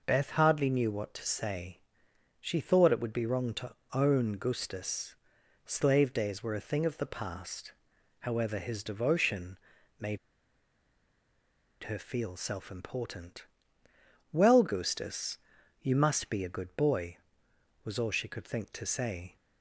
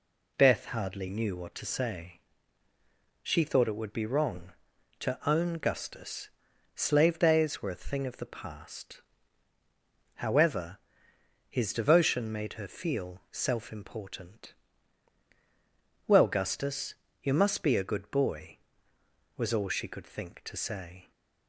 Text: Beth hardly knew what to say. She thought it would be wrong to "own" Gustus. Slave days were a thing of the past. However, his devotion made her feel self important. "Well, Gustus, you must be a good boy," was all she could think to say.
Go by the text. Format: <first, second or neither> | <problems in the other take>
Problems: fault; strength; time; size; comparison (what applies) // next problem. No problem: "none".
second | pauses between "to" and "own"; slight; at 3.7 s; 0.20 s long // pauses between "devotion" and "made"; at 9.5 s; 0.42 s long // pauses between "made" and "her"; strong; at 10.1 s; 1.6 s long